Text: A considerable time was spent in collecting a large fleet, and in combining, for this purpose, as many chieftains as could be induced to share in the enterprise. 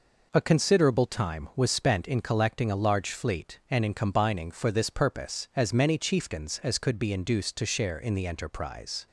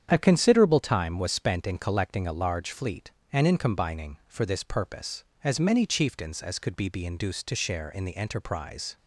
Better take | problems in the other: first | starts louder than the rest; strong; until 1.1 s; 8.5 dB // says "be" twice; at 6.8 s

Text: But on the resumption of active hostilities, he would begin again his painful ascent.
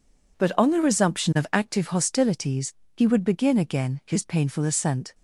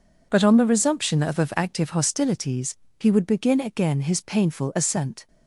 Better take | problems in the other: first | says "of" twice; at 1.3 s

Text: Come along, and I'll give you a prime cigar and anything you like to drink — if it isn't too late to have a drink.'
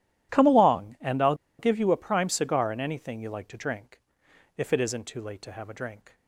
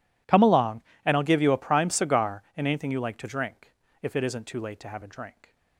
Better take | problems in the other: second | pauses between "I'll" and "give"; slight; at 1.3 s; 0.24 s long

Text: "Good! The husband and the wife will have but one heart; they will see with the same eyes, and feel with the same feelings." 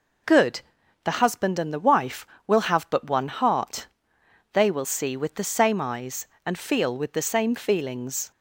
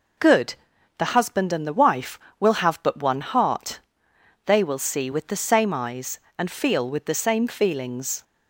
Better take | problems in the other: neither | none

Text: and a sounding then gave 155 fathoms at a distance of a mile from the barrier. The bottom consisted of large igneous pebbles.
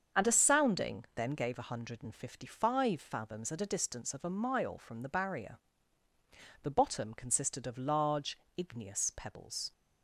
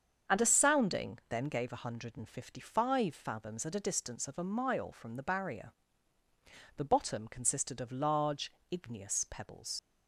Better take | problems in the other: first | starts louder than the rest; until 1.4 s; 7 dB; also in the first // pauses between "large" and "igneous"; slight; at 8.4 s; 0.22 s long; slight in the first // leaves "pebbles" unfinished; at 9.7 s; 70 ms

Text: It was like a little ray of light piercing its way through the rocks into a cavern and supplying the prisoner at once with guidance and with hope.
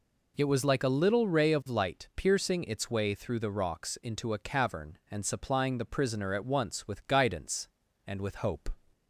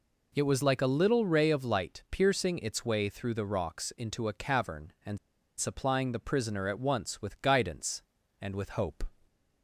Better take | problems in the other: first | pauses between "and" and "supplying"; at 5.1 s; 0.40 s long

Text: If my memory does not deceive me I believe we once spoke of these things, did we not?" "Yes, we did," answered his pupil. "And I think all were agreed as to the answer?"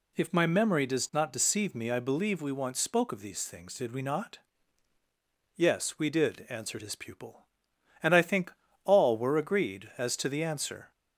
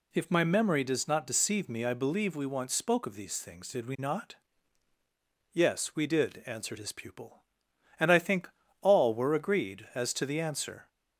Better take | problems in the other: neither | pauses between "think" and "all"; slight; the same in both

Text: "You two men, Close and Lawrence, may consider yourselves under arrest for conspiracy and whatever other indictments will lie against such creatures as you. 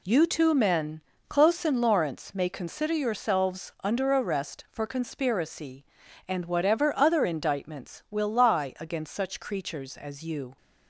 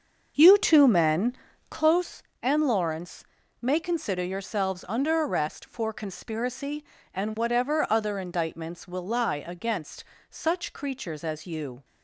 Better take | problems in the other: first | starts louder than the rest; until 2.0 s; 6.5 dB // pauses between "against" and "such"; slight; at 10.0 s; 0.24 s long

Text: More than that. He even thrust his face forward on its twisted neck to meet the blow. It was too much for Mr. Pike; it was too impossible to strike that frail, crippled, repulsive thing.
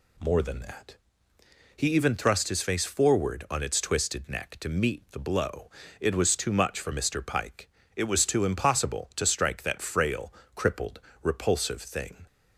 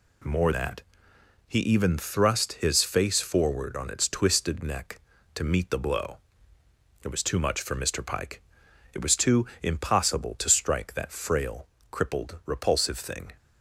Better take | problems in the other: first | skips "than"; at 0.5 s // pauses between "too" and "impossible"; slight; at 9.4 s; 0.16 s long

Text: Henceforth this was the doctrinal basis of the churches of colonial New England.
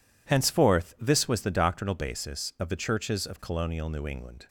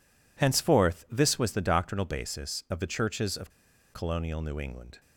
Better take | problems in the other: first | pauses between "of" and "colonial"; at 3.4 s; 0.43 s long

